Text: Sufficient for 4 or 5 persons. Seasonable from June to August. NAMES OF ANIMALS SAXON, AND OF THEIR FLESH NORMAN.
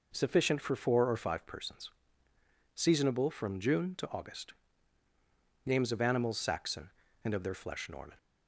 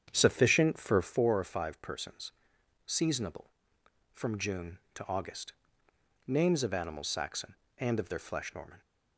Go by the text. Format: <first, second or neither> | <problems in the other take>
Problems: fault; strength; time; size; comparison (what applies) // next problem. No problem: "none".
first | starts louder than the rest; strong; until 1.1 s; 8.5 dB